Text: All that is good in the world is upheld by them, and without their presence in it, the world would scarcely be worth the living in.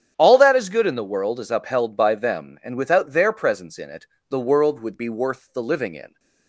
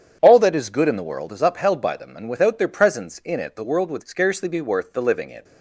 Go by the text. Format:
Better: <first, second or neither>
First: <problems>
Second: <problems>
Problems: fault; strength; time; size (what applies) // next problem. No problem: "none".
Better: second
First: starts louder than the rest; strong; until 1.1 s; 9 dB // skips "scarcely"; at 4.9 s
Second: starts louder than the rest; strong; until 1.2 s; 8.5 dB